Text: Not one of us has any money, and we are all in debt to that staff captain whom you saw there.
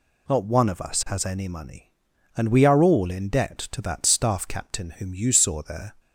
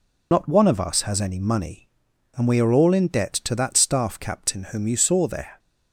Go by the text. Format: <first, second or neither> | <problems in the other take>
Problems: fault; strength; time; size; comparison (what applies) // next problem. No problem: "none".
first | loses the start of "Not"; at 0.3 s; 60 ms